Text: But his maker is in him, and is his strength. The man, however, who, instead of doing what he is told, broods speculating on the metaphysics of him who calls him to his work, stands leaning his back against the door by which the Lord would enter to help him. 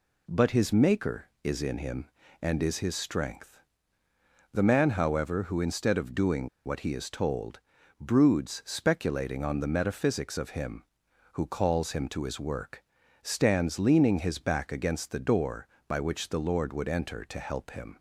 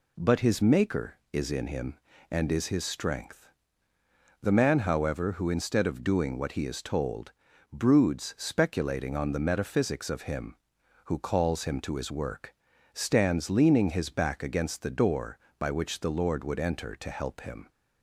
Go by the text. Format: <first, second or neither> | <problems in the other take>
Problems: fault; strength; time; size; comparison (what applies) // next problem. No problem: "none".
second | pauses between "doing" and "what"; slight; at 6.4 s; 0.17 s long